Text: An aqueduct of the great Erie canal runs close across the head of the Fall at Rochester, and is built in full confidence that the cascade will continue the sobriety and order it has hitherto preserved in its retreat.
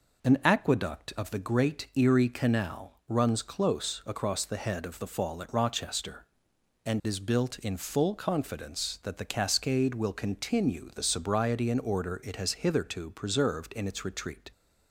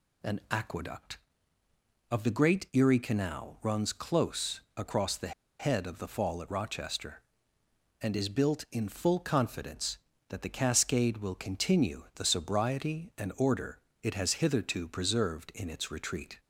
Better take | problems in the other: first | pauses between "close" and "across"; slight; at 4.5 s; 0.18 s long // pauses between "the" and "head"; slight; at 5.3 s; 0.25 s long // pauses between "order" and "it"; slight; at 13.7 s; 0.22 s long

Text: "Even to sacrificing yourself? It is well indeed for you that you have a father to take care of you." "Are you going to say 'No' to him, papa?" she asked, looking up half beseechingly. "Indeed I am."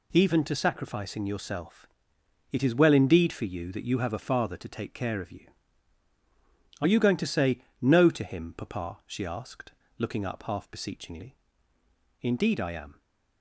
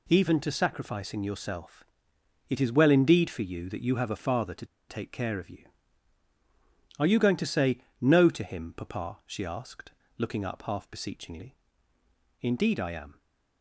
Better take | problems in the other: first | pauses between "to" and "take"; slight; at 4.6 s; 0.22 s long // pauses between "say" and "No"; slight; at 7.7 s; 0.20 s long; slight in the first

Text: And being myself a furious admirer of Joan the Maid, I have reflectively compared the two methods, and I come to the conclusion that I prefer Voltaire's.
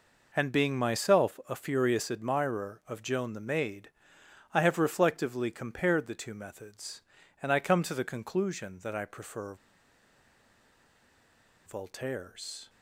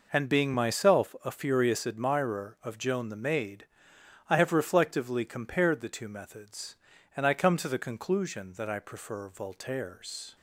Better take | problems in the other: second | pauses between "prefer" and "Voltaire's"; strong; at 9.5 s; 2.1 s long

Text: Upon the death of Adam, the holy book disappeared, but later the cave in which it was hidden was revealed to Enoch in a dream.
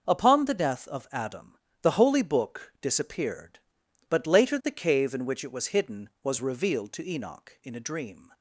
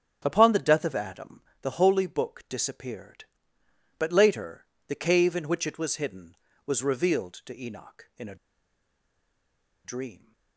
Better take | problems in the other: first | starts louder than the rest; strong; until 1.2 s; 8 dB // pauses between "later" and "the"; slight; at 4.6 s; 0.22 s long // pauses between "a" and "dream"; strong; at 8.3 s; 1.4 s long

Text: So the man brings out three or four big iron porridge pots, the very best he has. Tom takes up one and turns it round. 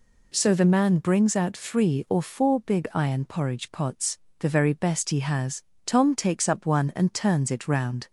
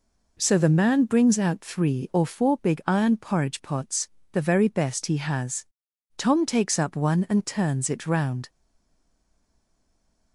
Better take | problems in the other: first | stays silent after the last word; noticeable; from 8.4 s on; 1.9 s long

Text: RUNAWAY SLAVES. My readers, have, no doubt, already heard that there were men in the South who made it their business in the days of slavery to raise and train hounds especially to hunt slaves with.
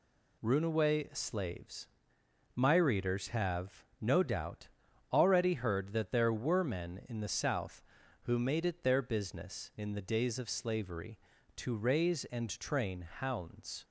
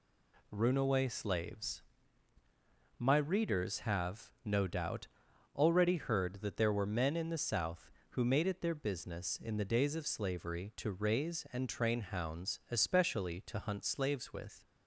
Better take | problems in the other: second | stops before "especially to hunt slaves with"; at 13.8 s

